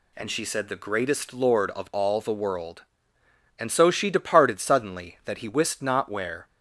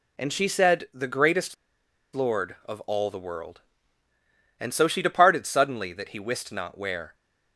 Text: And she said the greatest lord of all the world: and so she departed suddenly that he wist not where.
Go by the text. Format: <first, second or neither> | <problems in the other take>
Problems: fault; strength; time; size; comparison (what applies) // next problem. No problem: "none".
first | pauses between "greatest" and "lord"; noticeable; at 1.5 s; 0.59 s long